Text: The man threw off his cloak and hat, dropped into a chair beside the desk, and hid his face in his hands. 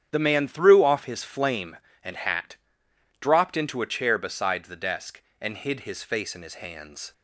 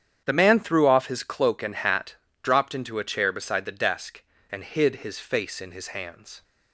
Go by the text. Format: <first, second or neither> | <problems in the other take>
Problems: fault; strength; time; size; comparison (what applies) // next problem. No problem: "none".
second | starts louder than the rest; strong; until 1.1 s; 9 dB; strong in the second // says "flame" for "cloak"; at 1.2 s